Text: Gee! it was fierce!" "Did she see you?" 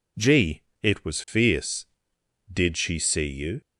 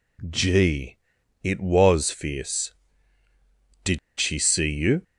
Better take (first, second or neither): first